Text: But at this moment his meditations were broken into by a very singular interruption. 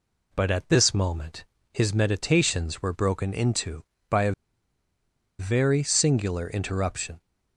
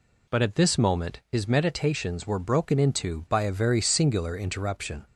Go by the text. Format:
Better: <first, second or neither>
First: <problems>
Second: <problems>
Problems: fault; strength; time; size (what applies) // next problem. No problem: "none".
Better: second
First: pauses between "moment" and "his"; slight; at 1.4 s; 0.30 s long // pauses between "a" and "very"; at 4.3 s; 1.0 s long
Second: none